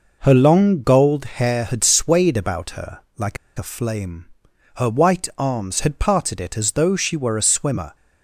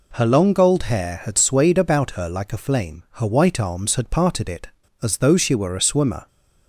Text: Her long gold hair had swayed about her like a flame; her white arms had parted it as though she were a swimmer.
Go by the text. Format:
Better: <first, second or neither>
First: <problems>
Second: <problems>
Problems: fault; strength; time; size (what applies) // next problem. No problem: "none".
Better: second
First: pauses between "her" and "like"; slight; at 2.9 s; 0.18 s long // pauses between "like" and "a"; slight; at 3.3 s; 0.21 s long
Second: none